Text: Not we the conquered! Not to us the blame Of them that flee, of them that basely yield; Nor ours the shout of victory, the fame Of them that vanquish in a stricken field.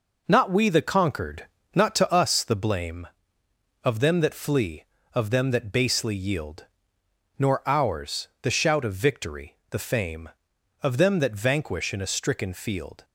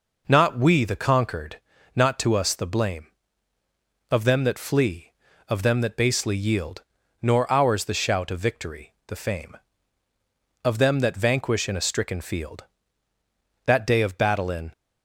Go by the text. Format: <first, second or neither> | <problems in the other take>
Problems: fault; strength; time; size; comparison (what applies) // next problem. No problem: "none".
first | goes on to say "That day of battle in"; noticeable; from 13.6 s on; 1.0 s long